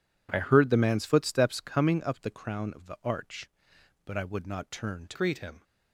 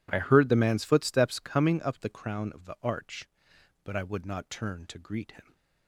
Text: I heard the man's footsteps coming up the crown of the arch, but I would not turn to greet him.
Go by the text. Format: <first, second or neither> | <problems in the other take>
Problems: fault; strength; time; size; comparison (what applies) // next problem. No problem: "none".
second | changes voice at "greet"; from 5.1 s on; 0.5 s long